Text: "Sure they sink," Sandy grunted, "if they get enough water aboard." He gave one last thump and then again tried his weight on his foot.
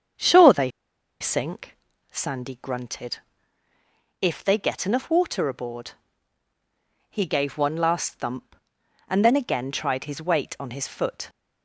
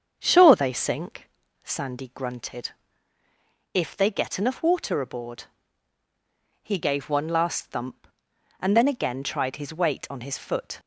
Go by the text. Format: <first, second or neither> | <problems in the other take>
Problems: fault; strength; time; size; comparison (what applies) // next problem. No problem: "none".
second | starts louder than the rest; strong; until 1.6 s; 7.5 dB; strong in the second // pauses between "they" and "sink"; noticeable; at 0.6 s; 0.51 s long